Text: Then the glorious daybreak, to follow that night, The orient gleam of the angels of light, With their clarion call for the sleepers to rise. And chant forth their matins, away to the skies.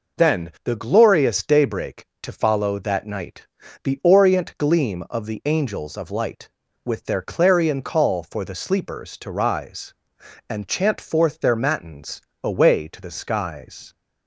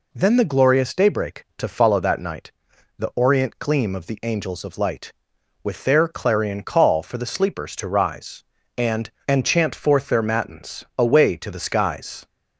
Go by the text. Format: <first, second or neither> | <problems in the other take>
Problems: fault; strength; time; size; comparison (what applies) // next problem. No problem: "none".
first | says "And" twice; at 9.2 s